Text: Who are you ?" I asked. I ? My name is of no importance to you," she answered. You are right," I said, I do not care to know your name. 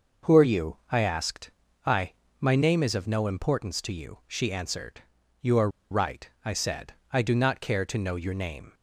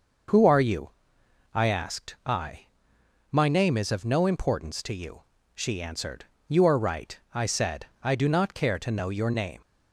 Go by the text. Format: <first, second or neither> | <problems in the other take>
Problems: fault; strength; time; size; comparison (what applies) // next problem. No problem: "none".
second | pauses between "are" and "right"; slight; at 5.6 s; 0.22 s long